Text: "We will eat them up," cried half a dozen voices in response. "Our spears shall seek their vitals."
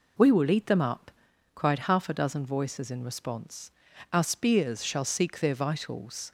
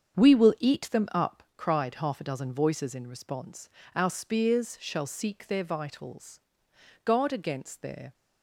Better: first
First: none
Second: starts louder than the rest; strong; until 1.2 s; 7.5 dB // goes on to say "Guard against their"; noticeable; from 7.0 s on; 1.1 s long

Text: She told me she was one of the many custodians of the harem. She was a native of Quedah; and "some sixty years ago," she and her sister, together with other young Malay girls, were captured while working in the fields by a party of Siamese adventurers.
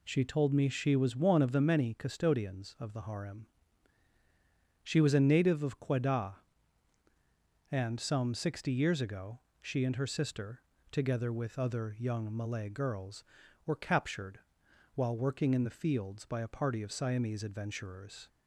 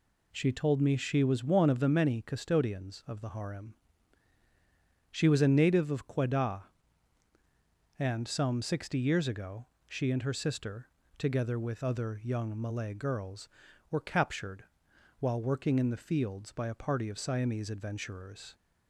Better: neither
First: pauses between "captured" and "while"; noticeable; at 14.3 s; 0.54 s long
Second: pauses between "captured" and "while"; noticeable; at 14.6 s; 0.54 s long

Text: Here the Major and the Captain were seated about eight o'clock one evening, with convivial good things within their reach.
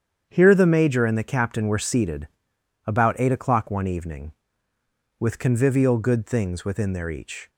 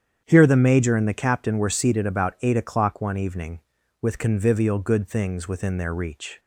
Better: second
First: starts louder than the rest; strong; until 1.3 s; 8.5 dB // pauses between "seated" and "about"; noticeable; at 2.2 s; 0.58 s long // says "each" for "reach"; at 7.0 s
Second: starts louder than the rest; strong; until 1.2 s; 8.5 dB

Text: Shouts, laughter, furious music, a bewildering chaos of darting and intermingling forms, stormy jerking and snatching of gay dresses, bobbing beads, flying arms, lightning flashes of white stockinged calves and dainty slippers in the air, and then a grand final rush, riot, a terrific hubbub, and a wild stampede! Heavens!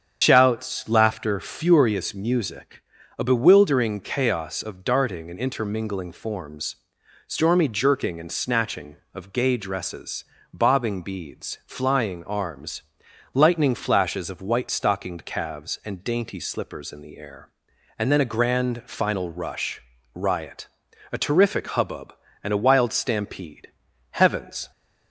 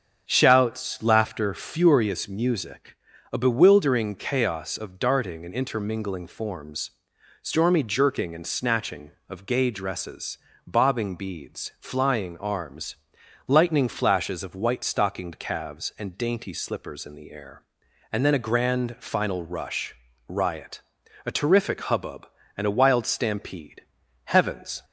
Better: second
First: loses the start of "Shouts"; at 0.2 s; 80 ms // starts louder than the rest; strong; until 1.2 s; 8 dB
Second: starts louder than the rest; until 1.2 s; 7 dB

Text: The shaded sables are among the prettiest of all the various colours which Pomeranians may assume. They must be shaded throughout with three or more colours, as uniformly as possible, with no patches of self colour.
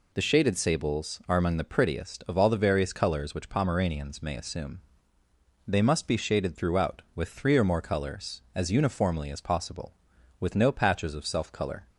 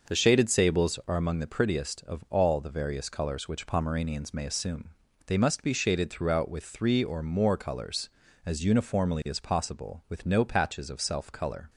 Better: first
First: none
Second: starts louder than the rest; noticeable; until 1.0 s; 6 dB

